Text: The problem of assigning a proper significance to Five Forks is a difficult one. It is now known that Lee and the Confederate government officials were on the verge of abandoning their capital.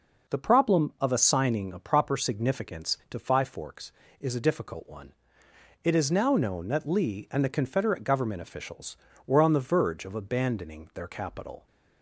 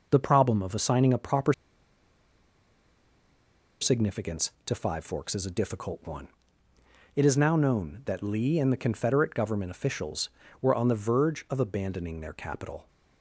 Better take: first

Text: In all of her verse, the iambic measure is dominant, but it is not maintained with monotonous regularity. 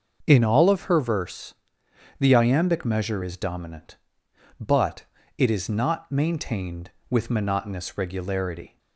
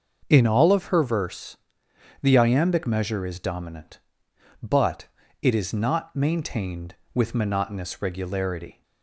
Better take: neither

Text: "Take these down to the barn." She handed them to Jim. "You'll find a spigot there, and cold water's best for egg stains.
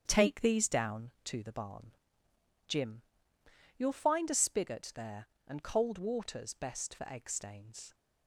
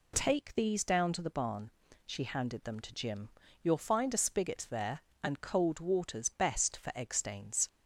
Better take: second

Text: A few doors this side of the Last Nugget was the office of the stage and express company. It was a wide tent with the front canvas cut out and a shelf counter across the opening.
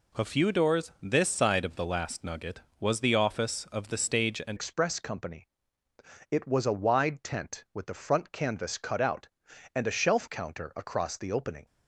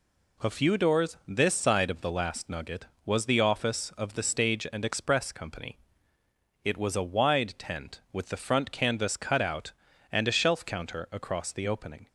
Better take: second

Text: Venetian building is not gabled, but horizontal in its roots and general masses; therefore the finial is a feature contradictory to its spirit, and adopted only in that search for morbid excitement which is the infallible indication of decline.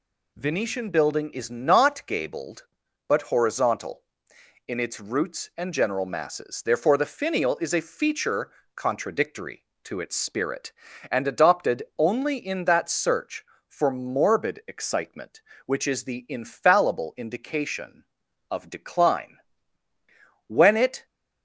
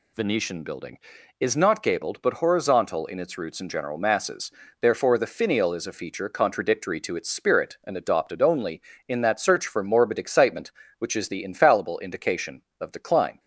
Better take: second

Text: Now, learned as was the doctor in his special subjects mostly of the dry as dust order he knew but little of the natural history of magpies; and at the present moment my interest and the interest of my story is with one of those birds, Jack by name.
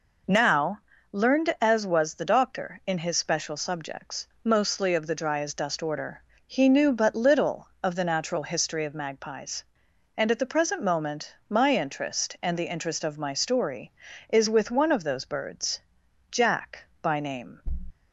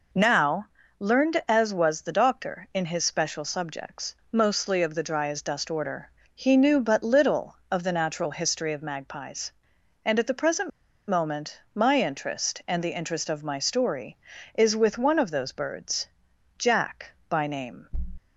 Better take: first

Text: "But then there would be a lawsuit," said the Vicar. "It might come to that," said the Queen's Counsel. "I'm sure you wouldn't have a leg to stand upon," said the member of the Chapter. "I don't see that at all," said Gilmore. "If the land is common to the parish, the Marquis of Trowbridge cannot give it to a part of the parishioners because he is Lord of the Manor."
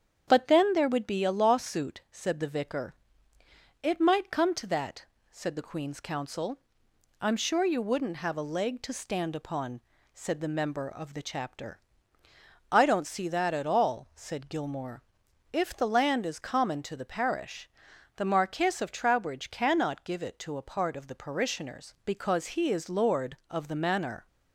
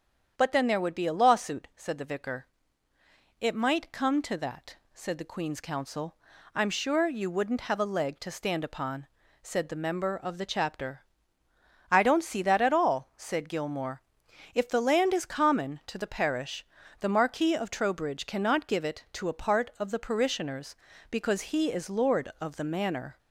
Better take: neither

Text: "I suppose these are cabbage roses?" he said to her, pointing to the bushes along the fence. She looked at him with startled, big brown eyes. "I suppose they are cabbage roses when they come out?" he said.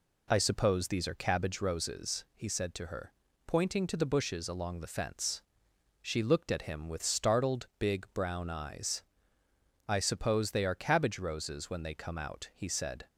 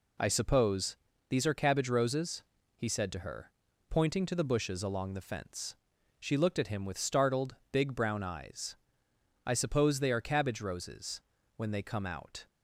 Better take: first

